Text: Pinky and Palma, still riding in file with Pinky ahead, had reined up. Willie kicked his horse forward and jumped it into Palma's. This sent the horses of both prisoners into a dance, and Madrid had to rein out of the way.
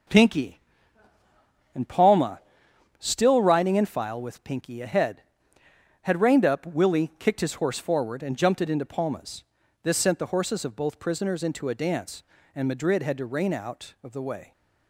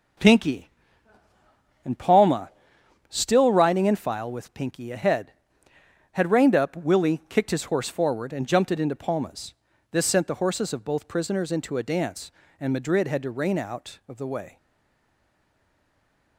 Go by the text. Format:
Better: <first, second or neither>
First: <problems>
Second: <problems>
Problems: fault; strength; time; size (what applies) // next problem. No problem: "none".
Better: first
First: starts louder than the rest; until 2.2 s; 6 dB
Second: starts louder than the rest; until 2.3 s; 6 dB // stays silent after the last word; noticeable; from 14.5 s on; 1.8 s long